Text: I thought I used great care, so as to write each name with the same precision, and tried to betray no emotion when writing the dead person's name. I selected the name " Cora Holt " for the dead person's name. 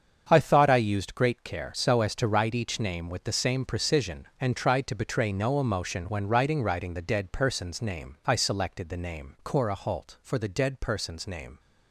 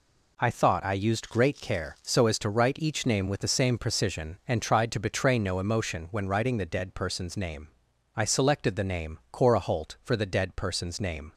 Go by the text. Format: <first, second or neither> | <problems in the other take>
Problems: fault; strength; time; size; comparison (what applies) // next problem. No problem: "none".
second | starts louder than the rest; strong; until 1.3 s; 7 dB // says "writing" twice; at 6.6 s